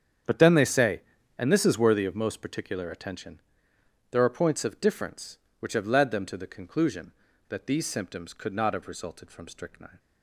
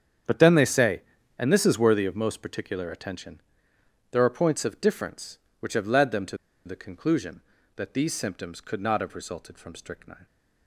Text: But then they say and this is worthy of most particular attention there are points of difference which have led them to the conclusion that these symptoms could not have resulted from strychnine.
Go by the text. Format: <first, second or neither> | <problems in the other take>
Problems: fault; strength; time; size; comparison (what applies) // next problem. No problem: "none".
first | starts louder than the rest; strong; until 1.6 s; 8 dB; strong in the first // pauses between "attention" and "there"; noticeable; at 3.4 s; 0.70 s long; noticeable in the first // pauses between "to" and "the"; slight; at 6.3 s; 0.28 s long